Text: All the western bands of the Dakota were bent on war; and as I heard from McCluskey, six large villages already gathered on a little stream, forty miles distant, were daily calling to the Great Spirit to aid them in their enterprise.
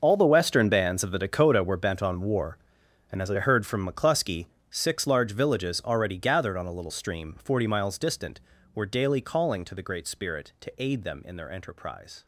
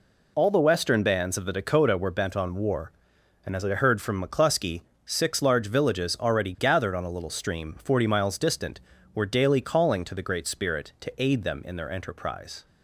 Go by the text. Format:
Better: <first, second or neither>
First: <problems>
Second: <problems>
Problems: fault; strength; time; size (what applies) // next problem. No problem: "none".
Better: second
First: gets quieter; strong; throughout; 15 dB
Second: none